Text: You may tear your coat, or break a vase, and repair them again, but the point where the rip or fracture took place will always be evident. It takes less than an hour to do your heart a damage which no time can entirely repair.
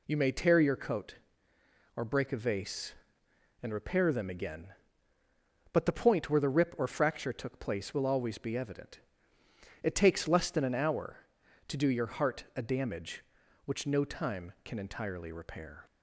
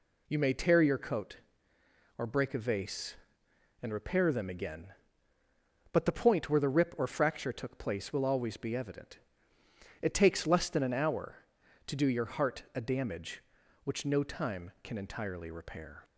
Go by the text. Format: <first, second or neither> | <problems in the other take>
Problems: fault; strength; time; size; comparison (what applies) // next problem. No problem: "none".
neither | none